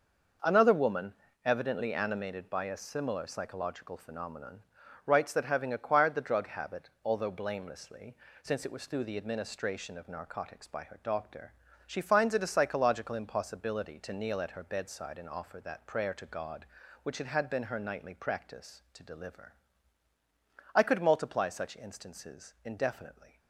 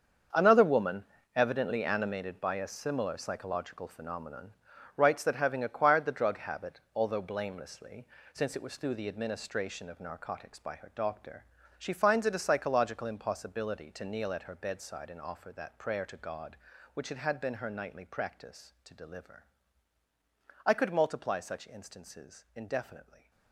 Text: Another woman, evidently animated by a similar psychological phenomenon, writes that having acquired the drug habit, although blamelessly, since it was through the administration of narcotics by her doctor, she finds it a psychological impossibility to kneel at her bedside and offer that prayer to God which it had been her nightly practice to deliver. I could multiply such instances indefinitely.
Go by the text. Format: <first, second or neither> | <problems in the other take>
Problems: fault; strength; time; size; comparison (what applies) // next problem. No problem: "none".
first | gets quieter; strong; throughout; 13 dB